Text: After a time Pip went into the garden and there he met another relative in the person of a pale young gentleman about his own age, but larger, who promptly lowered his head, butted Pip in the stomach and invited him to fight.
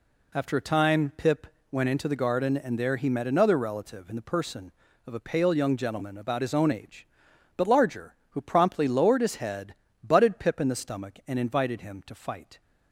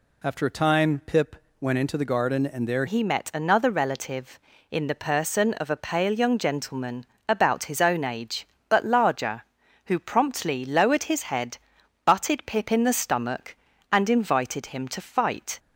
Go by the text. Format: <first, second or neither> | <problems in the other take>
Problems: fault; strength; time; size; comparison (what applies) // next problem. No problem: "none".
first | pauses between "Pip" and "went"; slight; at 1.3 s; 0.24 s long; slight in the first // changes voice at "he"; from 2.8 s on; 12.7 s long // pauses between "gentleman" and "about"; slight; at 7.0 s; 0.20 s long